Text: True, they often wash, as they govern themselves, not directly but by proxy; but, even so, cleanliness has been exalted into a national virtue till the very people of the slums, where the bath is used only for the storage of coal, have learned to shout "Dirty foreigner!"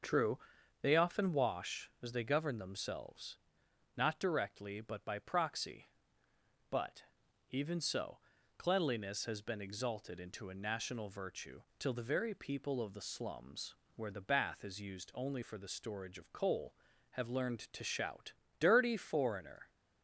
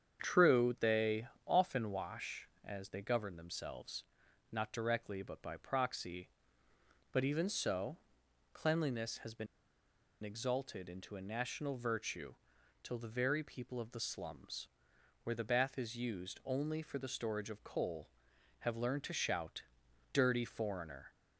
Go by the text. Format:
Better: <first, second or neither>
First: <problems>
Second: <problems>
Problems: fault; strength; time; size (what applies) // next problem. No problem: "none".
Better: first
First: starts louder than the rest; until 1.4 s; 6 dB // pauses between "virtue" and "till"; slight; at 11.6 s; 0.18 s long // pauses between "shout" and "Dirty"; slight; at 18.3 s; 0.24 s long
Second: starts louder than the rest; strong; until 1.2 s; 8 dB // pauses between "they" and "often"; slight; at 1.2 s; 0.20 s long // pauses between "been" and "exalted"; noticeable; at 9.4 s; 0.77 s long // pauses between "virtue" and "till"; noticeable; at 12.3 s; 0.48 s long // pauses between "shout" and "Dirty"; noticeable; at 19.6 s; 0.52 s long